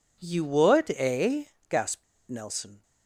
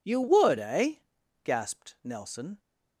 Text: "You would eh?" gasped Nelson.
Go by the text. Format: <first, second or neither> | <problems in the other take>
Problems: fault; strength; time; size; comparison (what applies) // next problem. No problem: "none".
second | pauses between "gasped" and "Nelson"; slight; at 2.0 s; 0.24 s long